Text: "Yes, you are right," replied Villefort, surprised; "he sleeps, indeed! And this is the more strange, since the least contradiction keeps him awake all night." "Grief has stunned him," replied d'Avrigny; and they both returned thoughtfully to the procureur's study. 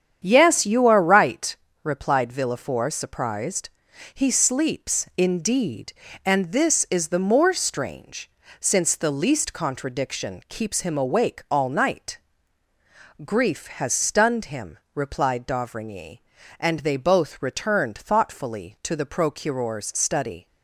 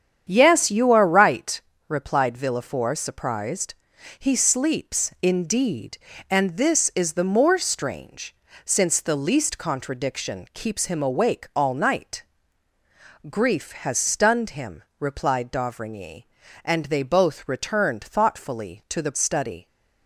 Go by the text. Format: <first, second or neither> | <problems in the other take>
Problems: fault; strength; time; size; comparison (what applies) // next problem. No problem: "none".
first | starts louder than the rest; strong; until 1.3 s; 8.5 dB; strong in the first // skips "procureur's"; at 19.1 s